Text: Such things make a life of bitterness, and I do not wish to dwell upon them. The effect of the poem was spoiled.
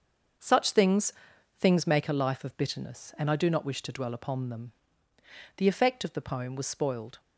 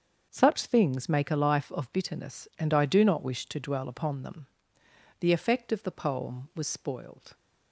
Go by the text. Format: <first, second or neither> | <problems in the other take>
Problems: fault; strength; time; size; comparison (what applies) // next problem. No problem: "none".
second | starts louder than the rest; until 1.8 s; 6.5 dB; also in the second // says "things" twice; at 1.5 s